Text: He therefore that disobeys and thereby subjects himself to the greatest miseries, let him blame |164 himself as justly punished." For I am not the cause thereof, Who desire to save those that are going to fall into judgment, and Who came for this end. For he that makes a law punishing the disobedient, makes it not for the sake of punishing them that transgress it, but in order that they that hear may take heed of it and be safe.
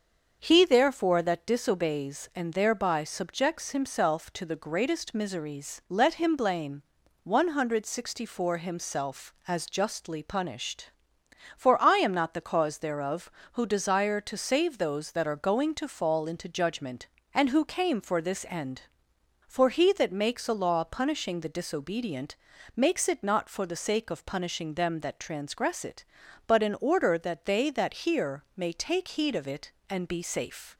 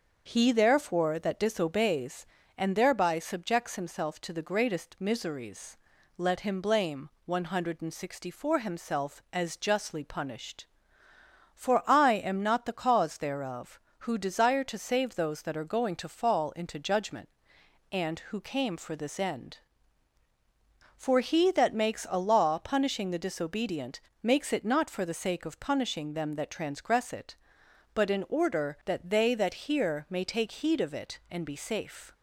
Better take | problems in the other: neither | starts louder than the rest; the same in both

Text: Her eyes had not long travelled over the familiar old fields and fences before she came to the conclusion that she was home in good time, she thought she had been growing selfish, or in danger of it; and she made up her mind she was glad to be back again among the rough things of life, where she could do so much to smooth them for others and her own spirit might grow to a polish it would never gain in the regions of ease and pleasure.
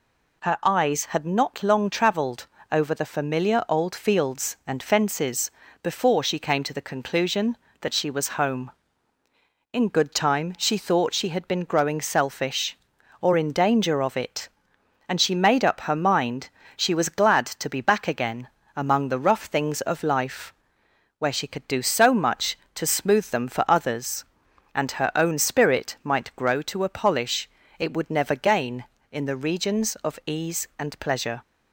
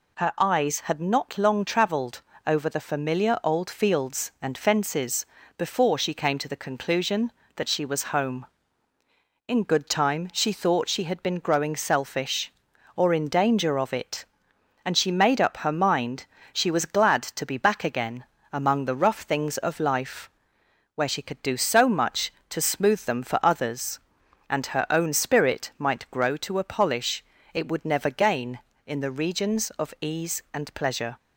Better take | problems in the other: neither | pauses between "travelled" and "over"; slight; the same in both // pauses between "fences" and "before"; slight; the same in both // pauses between "mind" and "she"; slight; the same in both // pauses between "again" and "among"; slight; the same in both // pauses between "polish" and "it"; slight; the same in both

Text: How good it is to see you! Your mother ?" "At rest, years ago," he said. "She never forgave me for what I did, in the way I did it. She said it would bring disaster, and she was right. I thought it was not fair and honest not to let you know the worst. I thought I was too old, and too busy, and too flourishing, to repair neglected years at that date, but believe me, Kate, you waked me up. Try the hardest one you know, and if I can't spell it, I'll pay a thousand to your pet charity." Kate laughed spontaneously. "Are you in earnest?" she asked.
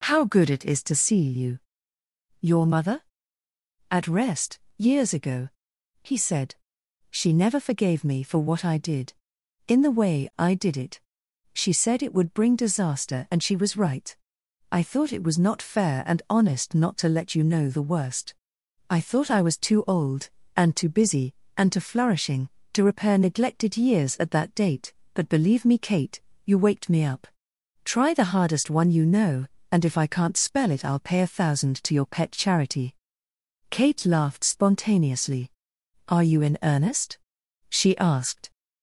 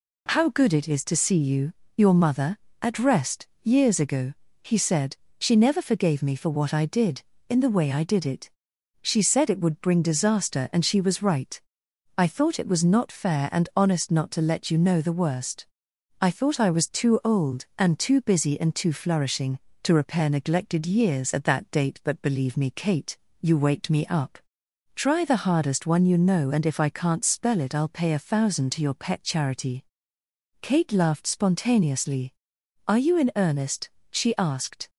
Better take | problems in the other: second | gets louder; slight; throughout; 3.5 dB

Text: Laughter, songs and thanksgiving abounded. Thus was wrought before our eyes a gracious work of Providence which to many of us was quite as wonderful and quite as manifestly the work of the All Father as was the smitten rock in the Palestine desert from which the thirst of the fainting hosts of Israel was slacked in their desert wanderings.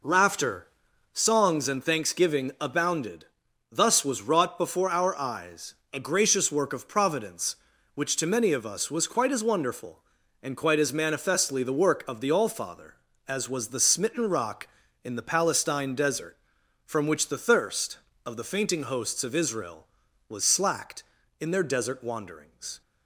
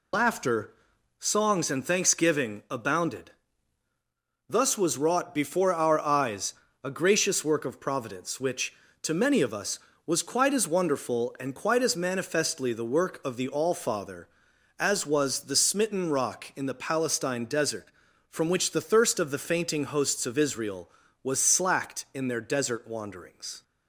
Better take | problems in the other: first | loses the start of "Laughter"; at 0.1 s; 55 ms // pauses between "eyes" and "a"; slight; at 6.5 s; 0.28 s long; slight in the first

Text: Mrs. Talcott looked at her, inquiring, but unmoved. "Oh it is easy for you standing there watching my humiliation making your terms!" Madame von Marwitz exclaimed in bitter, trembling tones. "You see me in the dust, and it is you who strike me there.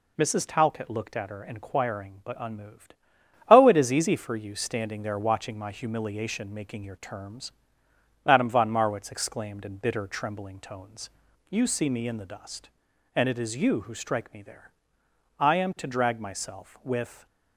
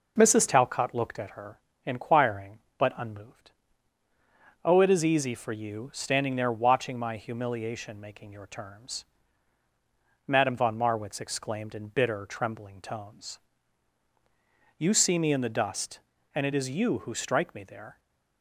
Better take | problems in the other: second | goes on to say "I am to drag myself with"; strong; from 15.3 s on; 1.8 s long

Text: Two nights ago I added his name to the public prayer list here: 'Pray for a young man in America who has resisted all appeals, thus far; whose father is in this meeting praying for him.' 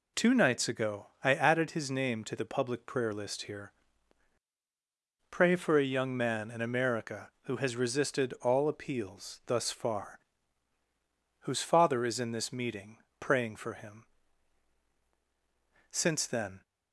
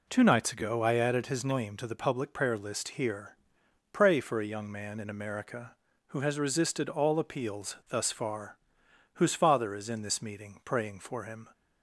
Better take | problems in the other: second | pauses between "ago" and "I"; slight; at 1.0 s; 0.16 s long // pauses between "meeting" and "praying"; slight; at 12.9 s; 0.22 s long // goes on to say "Since then"; noticeable; from 15.9 s on; 0.70 s long

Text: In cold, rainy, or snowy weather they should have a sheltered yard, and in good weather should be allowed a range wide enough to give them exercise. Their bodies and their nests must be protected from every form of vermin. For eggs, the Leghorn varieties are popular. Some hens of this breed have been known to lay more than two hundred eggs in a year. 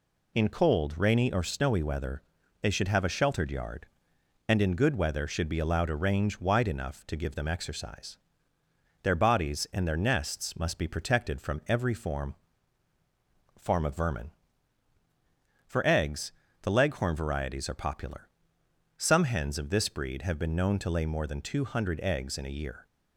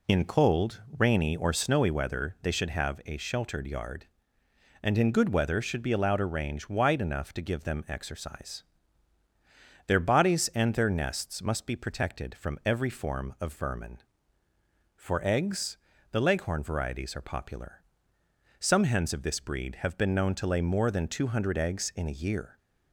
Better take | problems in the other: second | pauses between "weather" and "they"; at 2.2 s; 0.40 s long // says "form" twice; at 13.5 s

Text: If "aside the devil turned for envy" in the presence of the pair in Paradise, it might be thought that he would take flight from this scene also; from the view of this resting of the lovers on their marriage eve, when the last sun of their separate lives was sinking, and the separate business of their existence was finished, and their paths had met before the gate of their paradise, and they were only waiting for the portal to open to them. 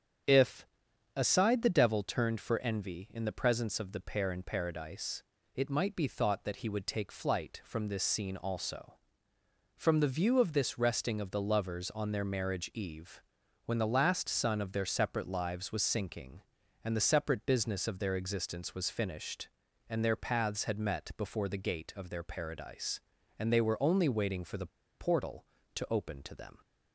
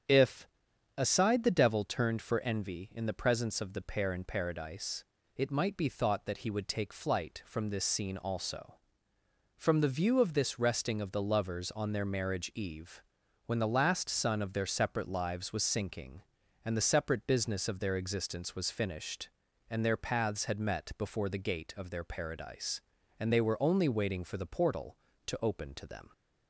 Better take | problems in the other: second | starts louder than the rest; strong; until 1.7 s; 7.5 dB; strong in the second // pauses between "If" and "aside"; noticeable; at 0.6 s; 0.48 s long; noticeable in the second // pauses between "the" and "portal"; slight; at 24.6 s; 0.31 s long

